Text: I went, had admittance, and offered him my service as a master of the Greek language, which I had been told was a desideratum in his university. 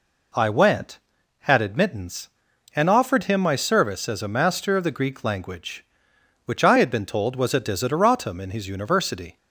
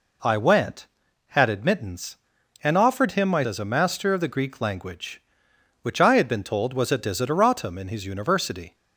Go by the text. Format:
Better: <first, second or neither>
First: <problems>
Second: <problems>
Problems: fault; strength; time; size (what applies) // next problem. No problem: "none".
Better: first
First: none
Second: skips "service"; at 3.4 s